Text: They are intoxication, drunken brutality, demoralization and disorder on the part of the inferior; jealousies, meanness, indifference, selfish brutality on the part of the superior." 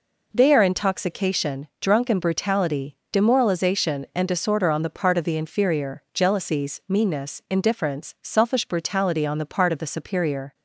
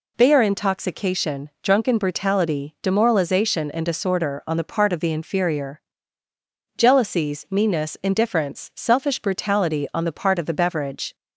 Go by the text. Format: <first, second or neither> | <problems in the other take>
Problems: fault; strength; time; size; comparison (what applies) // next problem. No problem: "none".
first | says "beverage" for "superior"; at 10.5 s